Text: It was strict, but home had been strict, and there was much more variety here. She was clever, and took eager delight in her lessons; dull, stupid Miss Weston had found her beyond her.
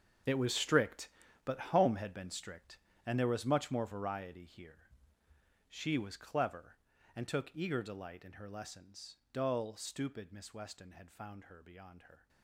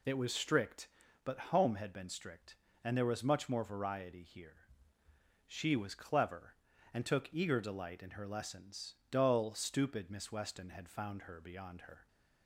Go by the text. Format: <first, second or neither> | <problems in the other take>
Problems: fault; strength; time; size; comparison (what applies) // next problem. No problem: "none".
second | gets quieter; strong; throughout; 15 dB